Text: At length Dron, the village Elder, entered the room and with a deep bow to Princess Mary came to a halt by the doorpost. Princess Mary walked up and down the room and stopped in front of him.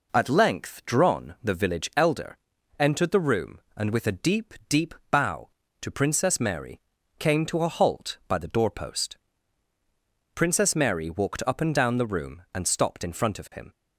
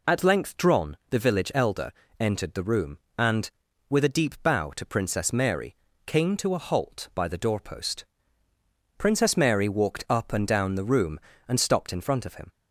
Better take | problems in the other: second | says "deep" twice; at 4.6 s // pauses between "Mary" and "came"; at 6.7 s; 0.40 s long; slight in the second

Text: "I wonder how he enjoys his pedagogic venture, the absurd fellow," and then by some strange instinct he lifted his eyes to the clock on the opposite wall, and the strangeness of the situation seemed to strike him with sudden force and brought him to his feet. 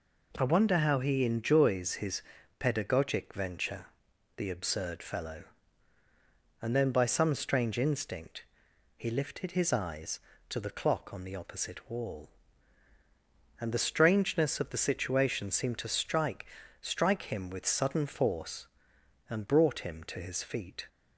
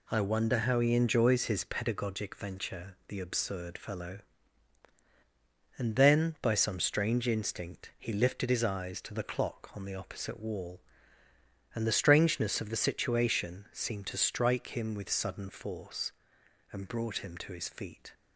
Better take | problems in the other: second | pauses between "his" and "pedagogic"; slight; at 2.2 s; 0.36 s long // pauses between "instinct" and "he"; noticeable; at 8.4 s; 0.52 s long // says "strike" twice; at 16.7 s

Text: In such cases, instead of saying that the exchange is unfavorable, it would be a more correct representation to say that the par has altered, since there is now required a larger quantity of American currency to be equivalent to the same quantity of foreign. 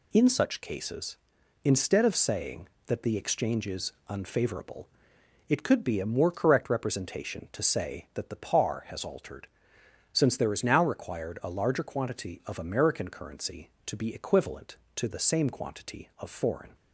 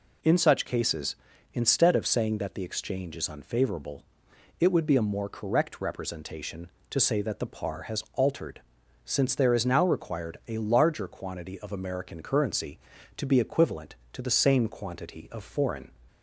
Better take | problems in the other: second | pauses between "is" and "unfavorable"; slight; at 3.9 s; 0.16 s long // says "could" for "would"; at 5.6 s

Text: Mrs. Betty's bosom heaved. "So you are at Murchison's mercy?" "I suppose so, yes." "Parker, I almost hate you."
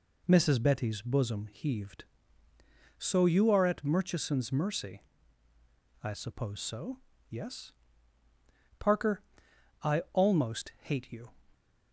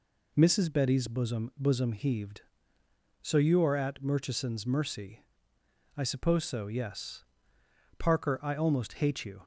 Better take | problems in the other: first | says "bosom" twice; at 1.5 s

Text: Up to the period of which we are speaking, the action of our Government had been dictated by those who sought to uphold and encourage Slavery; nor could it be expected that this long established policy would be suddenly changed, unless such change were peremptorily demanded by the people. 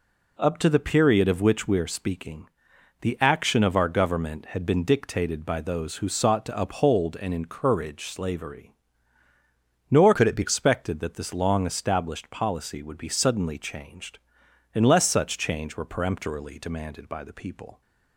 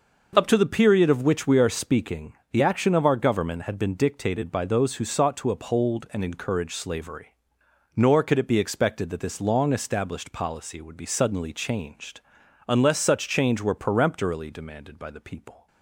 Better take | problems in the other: second | changes voice from "could" to "be"; from 10.1 to 10.4 s; 0.3 s long

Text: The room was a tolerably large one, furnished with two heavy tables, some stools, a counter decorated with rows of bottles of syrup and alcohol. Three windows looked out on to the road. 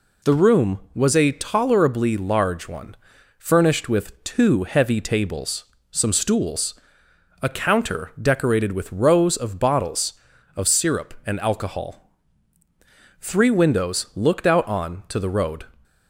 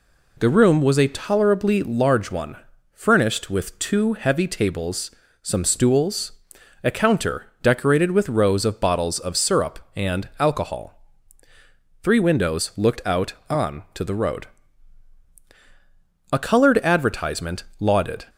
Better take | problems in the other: first | goes on to say "A coloured advertisement lauded"; strong; from 16.2 s on; 1.9 s long

